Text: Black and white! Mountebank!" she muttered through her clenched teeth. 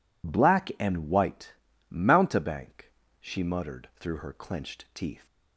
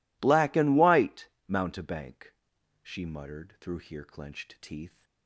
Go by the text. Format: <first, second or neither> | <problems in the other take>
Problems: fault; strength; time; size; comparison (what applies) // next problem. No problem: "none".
first | says "here" for "her"; at 3.7 s